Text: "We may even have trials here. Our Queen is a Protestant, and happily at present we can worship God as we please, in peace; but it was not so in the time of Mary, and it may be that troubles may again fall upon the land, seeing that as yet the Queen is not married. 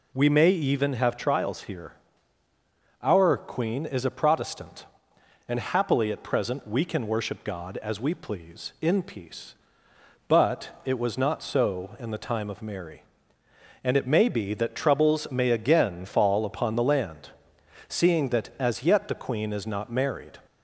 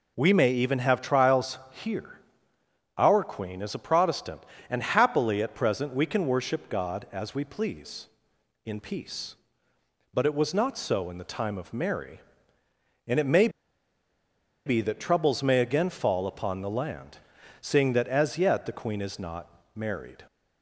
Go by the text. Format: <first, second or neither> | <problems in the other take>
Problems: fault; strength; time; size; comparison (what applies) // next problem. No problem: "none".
first | pauses between "may" and "be"; at 13.4 s; 1.1 s long // pauses between "not" and "married"; slight; at 19.4 s; 0.28 s long